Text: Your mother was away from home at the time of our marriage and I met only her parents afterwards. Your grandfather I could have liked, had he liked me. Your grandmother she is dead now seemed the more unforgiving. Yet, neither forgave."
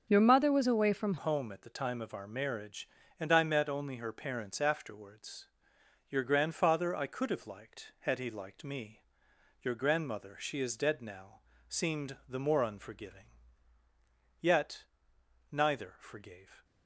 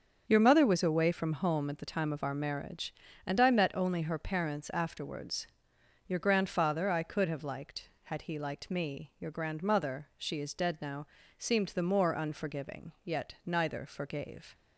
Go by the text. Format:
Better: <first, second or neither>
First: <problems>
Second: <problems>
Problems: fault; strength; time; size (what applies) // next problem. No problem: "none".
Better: second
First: starts louder than the rest; until 1.1 s; 7 dB // changes voice at "home"; from 1.1 s on; 15.5 s long // pauses between "now" and "seemed"; slight; at 11.4 s; 0.28 s long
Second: starts louder than the rest; until 1.2 s; 7 dB // pauses between "now" and "seemed"; slight; at 11.0 s; 0.32 s long